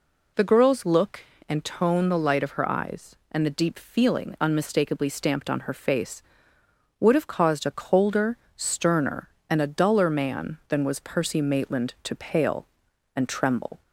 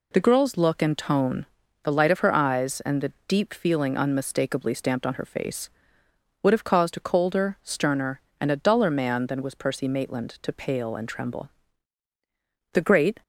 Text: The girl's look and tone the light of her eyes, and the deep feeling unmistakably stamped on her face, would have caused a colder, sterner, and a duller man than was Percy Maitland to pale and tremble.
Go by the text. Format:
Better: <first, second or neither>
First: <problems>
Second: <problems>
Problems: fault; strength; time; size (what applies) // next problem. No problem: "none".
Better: first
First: none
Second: pauses between "tone" and "the"; at 1.4 s; 0.38 s long // goes on to say "The great"; slight; from 12.7 s on; 0.48 s long